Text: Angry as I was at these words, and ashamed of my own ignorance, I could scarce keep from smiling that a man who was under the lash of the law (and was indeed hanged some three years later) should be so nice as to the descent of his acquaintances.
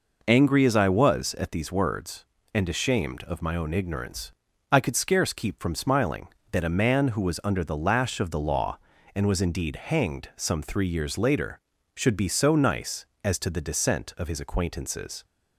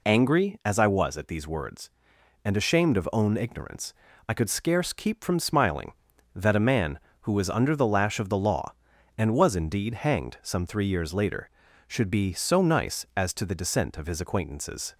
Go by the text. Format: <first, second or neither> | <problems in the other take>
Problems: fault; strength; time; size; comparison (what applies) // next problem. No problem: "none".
first | skips "my"; at 3.0 s